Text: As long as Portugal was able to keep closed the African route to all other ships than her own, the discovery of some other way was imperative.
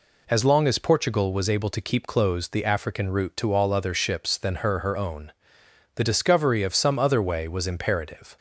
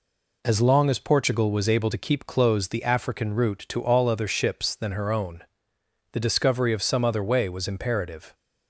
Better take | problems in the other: second | says "her" twice; at 4.7 s

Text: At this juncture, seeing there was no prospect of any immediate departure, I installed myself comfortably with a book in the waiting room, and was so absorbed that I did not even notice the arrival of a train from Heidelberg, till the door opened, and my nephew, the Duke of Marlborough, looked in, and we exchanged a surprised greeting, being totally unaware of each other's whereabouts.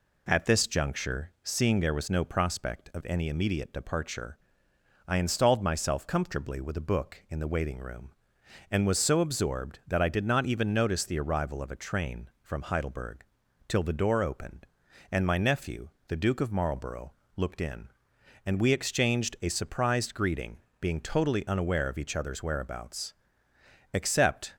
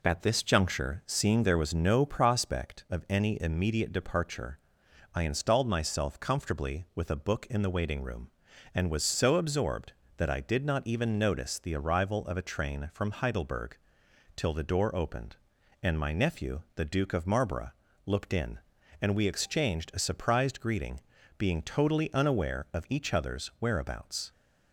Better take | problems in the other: second | goes on to say "Except"; noticeable; from 23.9 s on; 0.62 s long

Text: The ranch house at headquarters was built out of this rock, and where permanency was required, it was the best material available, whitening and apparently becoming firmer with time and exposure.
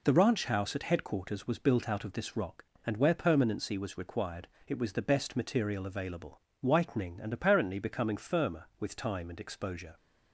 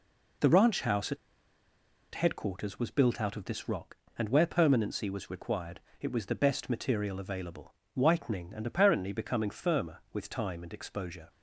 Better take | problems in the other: first | pauses between "at" and "headquarters"; at 1.1 s; 0.98 s long

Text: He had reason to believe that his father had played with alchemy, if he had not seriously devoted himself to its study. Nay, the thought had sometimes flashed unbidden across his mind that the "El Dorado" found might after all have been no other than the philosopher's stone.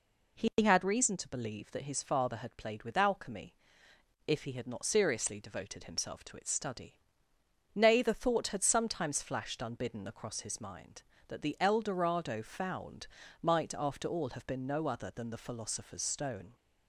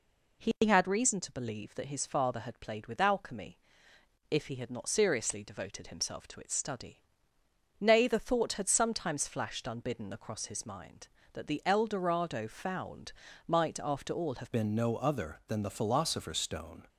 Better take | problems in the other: first | pauses between "found" and "might"; slight; at 13.1 s; 0.34 s long; slight in the first // changes voice at "been"; from 14.5 s on; 2.3 s long

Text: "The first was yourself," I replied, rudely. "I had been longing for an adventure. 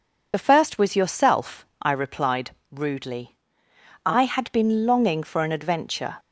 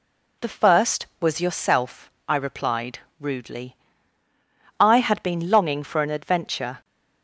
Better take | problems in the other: second | loses the start of "The"; at 0.3 s; 30 ms

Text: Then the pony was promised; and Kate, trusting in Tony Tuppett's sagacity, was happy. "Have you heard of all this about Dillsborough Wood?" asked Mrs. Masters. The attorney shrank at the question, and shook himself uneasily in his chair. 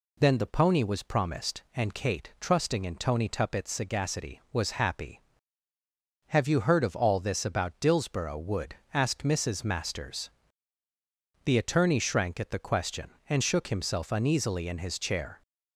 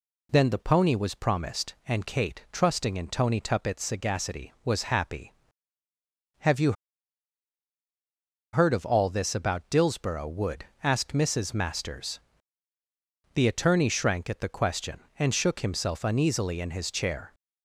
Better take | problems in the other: first | pauses between "you" and "heard"; strong; at 6.7 s; 1.8 s long

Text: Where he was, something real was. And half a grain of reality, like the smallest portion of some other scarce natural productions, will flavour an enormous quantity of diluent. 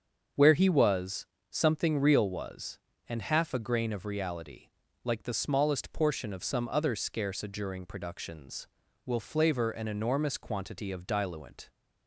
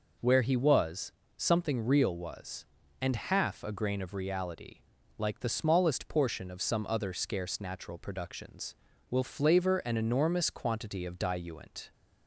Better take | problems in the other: second | starts louder than the rest; until 1.6 s; 7 dB // says "adjuring" for "natural"; at 7.4 s

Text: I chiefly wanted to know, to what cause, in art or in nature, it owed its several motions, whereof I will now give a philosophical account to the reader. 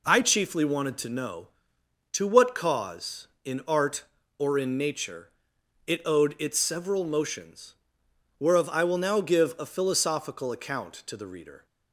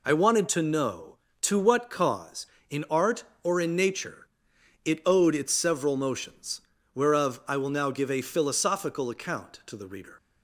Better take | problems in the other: first | skips "chiefly"; at 0.1 s

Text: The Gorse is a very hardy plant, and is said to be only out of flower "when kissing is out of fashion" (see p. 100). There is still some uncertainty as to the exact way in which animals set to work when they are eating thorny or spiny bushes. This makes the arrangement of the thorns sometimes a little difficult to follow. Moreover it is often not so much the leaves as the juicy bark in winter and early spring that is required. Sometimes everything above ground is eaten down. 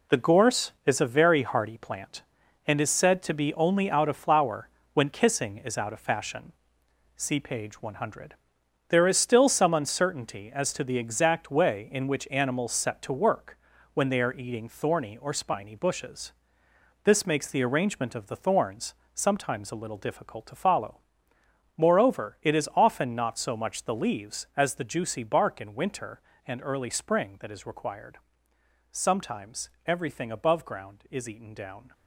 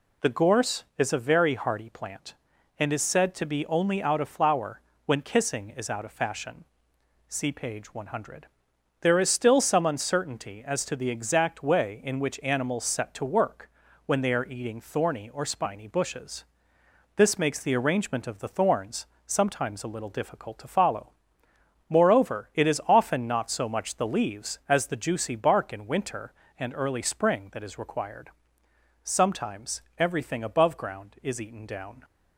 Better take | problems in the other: second | gets quieter; strong; throughout; 9 dB // pauses between "flower" and "when"; slight; at 4.6 s; 0.24 s long; slight in the second // pauses between "work" and "when"; slight; at 13.5 s; 0.36 s long; slight in the second // pauses between "thorns" and "sometimes"; slight; at 18.9 s; 0.22 s long; slight in the second // pauses between "Sometimes" and "everything"; slight; at 29.7 s; 0.16 s long; slight in the second

